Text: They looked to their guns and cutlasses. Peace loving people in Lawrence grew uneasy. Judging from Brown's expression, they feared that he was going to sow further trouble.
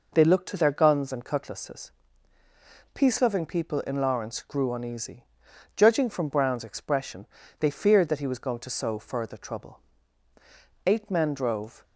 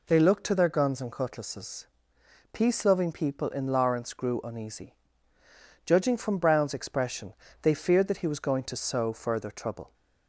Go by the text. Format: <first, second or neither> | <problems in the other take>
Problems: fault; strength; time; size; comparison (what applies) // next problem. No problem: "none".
second | goes on to say "Eight men drove"; noticeable; from 10.8 s on; 0.98 s long